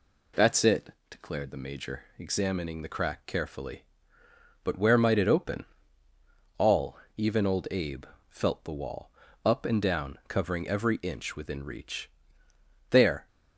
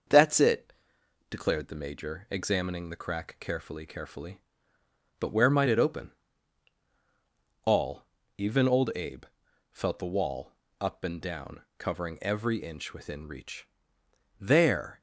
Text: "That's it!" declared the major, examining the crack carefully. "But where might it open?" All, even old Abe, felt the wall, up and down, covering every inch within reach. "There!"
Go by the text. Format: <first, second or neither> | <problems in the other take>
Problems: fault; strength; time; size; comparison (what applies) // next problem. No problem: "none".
first | starts louder than the rest; until 1.6 s; 6 dB // says "carefully" twice; at 3.8 s